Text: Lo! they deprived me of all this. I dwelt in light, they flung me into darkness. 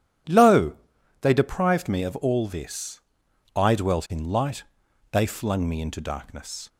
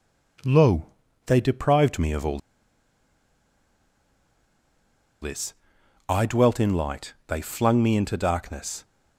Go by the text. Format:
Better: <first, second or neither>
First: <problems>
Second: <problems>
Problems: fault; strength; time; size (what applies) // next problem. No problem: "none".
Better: first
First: none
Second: pauses between "all" and "this"; strong; at 2.3 s; 2.8 s long